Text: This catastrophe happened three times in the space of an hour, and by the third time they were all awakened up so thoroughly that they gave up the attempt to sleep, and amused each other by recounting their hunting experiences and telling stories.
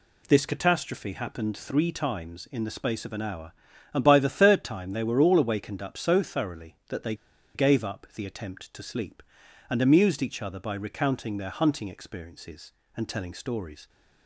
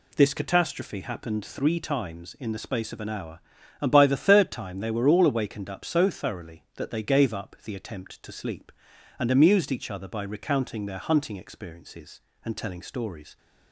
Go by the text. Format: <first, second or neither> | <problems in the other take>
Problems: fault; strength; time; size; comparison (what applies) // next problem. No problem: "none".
second | pauses between "they" and "gave"; at 7.1 s; 0.40 s long